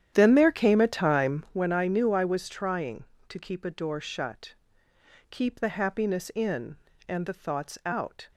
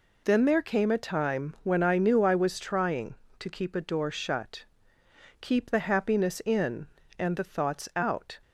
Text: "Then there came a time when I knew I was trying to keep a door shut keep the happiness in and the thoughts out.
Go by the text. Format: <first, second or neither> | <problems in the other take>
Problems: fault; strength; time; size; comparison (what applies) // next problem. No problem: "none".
second | starts louder than the rest; strong; until 1.6 s; 10 dB // pauses between "shut" and "keep"; noticeable; at 4.5 s; 0.76 s long; noticeable in the second